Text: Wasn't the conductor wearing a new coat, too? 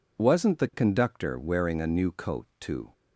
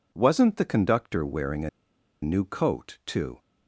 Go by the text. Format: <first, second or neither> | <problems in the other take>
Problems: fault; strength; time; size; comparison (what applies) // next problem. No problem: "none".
first | pauses between "a" and "new"; noticeable; at 1.6 s; 0.53 s long